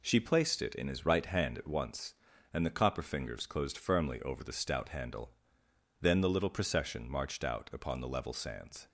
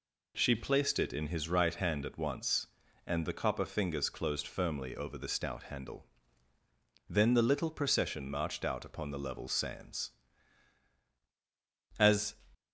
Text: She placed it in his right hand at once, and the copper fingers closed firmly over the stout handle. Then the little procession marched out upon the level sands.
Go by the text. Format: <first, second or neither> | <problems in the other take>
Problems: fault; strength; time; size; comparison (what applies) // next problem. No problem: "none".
first | goes on to say "As"; slight; from 11.9 s on; 0.38 s long